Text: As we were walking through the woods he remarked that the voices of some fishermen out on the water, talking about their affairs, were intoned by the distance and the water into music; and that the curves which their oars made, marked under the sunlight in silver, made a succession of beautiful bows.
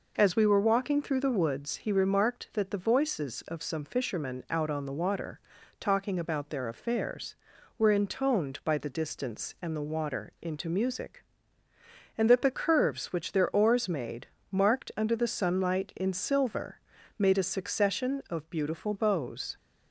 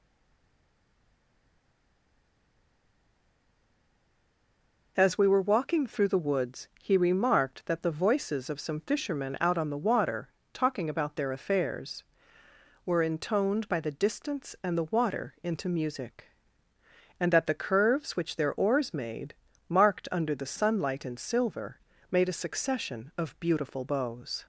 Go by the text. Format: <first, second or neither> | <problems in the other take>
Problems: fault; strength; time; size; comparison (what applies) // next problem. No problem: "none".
first | stays silent before the first word; strong; until 4.9 s; 4.9 s long